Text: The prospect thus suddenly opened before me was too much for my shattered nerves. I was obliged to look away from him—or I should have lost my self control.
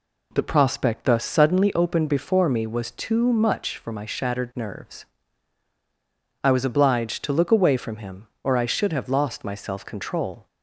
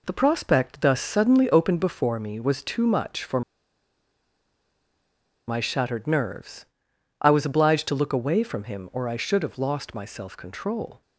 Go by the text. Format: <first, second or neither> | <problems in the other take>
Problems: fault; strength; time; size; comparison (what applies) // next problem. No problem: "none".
first | pauses between "for" and "my"; strong; at 3.4 s; 2.0 s long